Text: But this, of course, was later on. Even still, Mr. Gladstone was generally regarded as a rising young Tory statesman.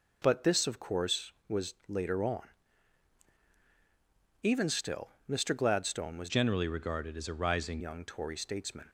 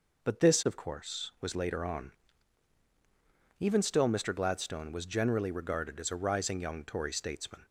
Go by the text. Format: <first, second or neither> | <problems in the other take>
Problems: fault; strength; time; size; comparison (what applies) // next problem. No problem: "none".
second | changes voice from "generally" to "rising"; from 6.2 to 7.7 s; 1.5 s long